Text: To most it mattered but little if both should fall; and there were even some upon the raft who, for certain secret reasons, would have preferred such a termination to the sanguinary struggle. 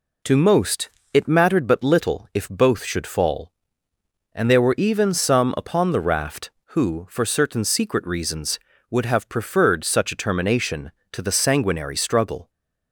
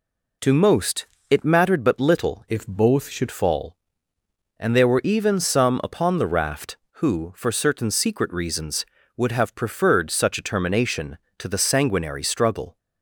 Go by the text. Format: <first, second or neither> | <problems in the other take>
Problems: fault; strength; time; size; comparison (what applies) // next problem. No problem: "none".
first | pauses between "most" and "it"; slight; at 1.0 s; 0.22 s long; slight in the first // changes voice from "if" to "should"; from 2.5 to 3.2 s; 0.7 s long